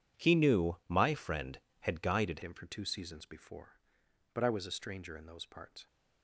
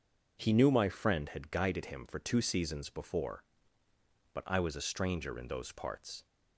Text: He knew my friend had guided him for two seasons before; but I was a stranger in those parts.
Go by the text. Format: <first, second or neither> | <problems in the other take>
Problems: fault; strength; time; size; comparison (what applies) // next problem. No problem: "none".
second | changes voice at "him"; from 2.4 s on; 3.4 s long